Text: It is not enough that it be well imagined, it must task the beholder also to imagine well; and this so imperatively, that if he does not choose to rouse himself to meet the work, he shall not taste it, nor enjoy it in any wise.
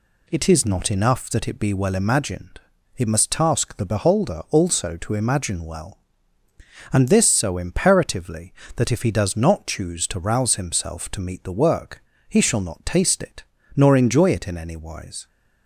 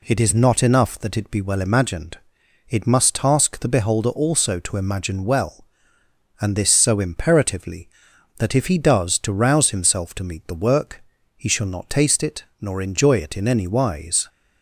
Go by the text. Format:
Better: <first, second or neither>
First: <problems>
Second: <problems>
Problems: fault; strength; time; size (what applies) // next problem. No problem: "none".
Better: first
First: none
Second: skips "not choose"; at 9.1 s